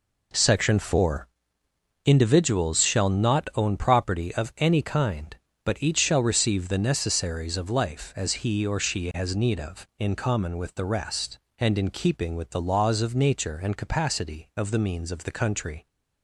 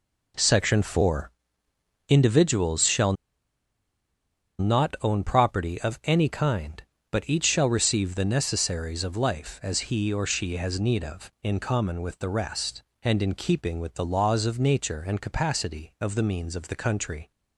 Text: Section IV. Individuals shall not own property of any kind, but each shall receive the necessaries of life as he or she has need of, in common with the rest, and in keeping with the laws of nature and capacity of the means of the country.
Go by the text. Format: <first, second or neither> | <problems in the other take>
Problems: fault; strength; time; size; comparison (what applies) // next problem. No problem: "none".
first | pauses between "shall" and "not"; strong; at 3.1 s; 1.4 s long